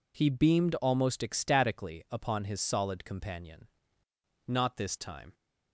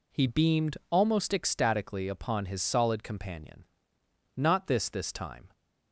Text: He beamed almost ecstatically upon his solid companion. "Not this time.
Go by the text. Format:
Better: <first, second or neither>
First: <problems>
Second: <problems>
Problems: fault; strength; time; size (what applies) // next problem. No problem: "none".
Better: first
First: none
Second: says "this" twice; at 4.8 s